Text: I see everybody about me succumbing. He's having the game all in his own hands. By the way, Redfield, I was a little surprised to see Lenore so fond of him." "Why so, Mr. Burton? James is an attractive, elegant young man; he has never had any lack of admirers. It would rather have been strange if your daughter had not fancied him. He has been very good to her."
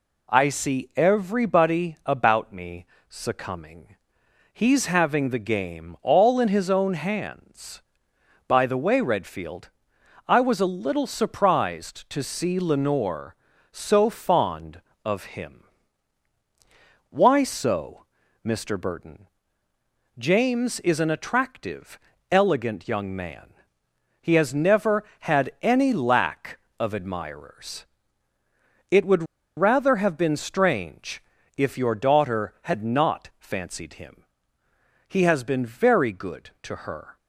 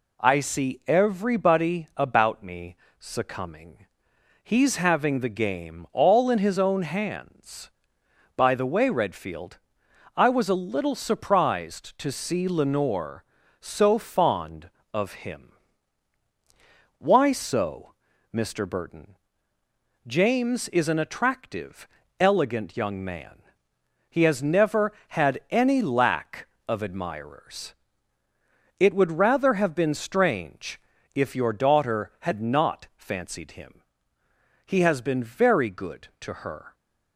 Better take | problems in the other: second | pauses between "me" and "succumbing"; slight; at 2.8 s; 0.24 s long; slight in the second // pauses between "would" and "rather"; slight; at 29.2 s; 0.33 s long // pauses between "strange" and "if"; slight; at 31.2 s; 0.34 s long; slight in the second

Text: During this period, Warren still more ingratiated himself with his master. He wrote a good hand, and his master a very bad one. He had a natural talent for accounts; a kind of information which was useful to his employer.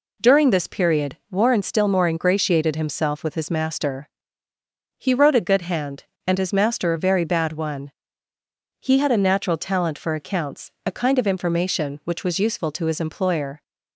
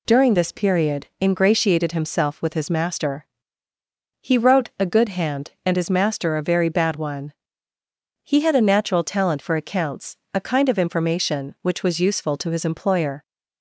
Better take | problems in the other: first | skips "Warren still more"; at 1.1 s

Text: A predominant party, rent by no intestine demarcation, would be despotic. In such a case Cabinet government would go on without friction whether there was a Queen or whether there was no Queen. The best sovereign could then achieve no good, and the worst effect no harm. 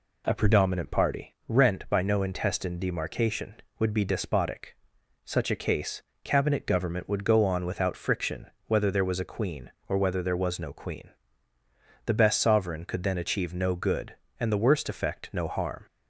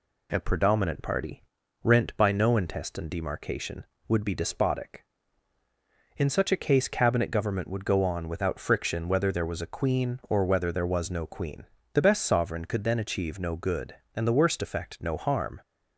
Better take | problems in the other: second | skips "In"; at 4.9 s // pauses between "case" and "Cabinet"; slight; at 6.0 s; 0.22 s long // pauses between "friction" and "whether"; slight; at 8.4 s; 0.16 s long

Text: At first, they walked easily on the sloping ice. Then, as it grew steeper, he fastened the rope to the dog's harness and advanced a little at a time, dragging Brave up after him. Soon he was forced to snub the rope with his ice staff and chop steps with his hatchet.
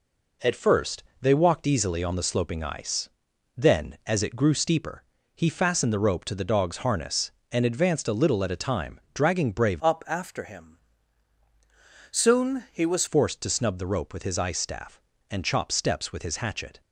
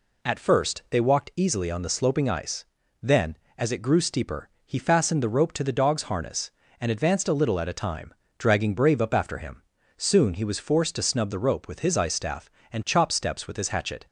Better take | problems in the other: second | changes voice from "up" to "was"; from 9.8 to 13.0 s; 3.2 s long

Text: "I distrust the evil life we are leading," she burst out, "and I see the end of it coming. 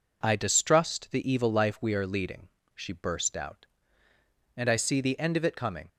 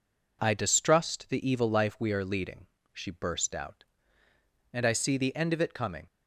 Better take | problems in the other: neither | none

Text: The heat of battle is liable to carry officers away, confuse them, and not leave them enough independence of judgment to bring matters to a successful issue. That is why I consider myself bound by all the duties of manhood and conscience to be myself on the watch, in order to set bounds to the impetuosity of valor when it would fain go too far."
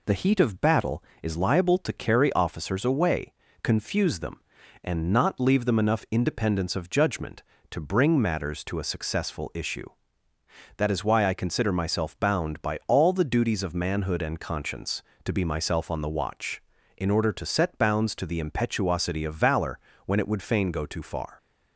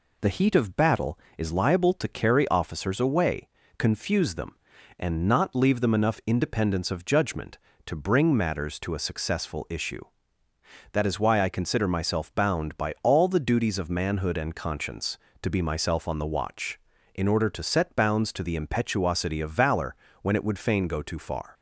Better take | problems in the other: neither | pauses between "valor" and "when"; slight; the same in both

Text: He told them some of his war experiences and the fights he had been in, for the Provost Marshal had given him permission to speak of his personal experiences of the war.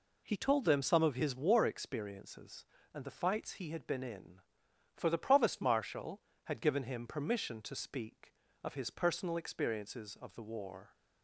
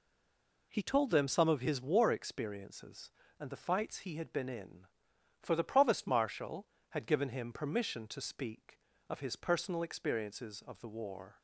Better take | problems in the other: first | stays silent before the first word; slight; until 0.7 s; 0.7 s long

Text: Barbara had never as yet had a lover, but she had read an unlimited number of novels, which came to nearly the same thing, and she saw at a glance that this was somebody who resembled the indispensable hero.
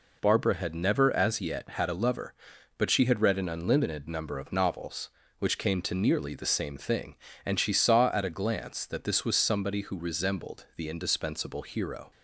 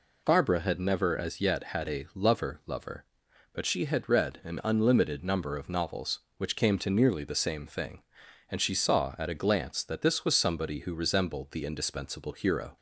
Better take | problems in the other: first | says "lover" twice; at 2.6 s

